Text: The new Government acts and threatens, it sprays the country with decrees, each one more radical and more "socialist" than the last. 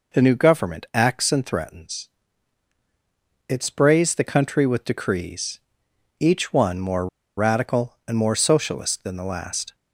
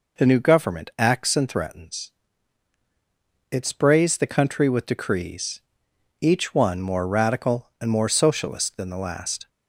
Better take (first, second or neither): second